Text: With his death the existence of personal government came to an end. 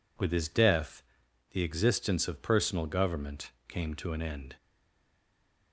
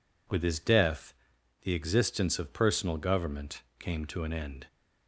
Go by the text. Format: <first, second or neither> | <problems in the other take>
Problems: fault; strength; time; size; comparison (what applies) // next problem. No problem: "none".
second | pauses between "death" and "the"; noticeable; at 1.0 s; 0.48 s long; noticeable in the second // pauses between "government" and "came"; slight; at 3.5 s; 0.16 s long; slight in the second // stays silent after the last word; from 4.5 s on; 1.2 s long